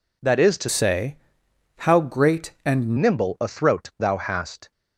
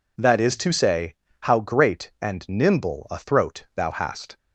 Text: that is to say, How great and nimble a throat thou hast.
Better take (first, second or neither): second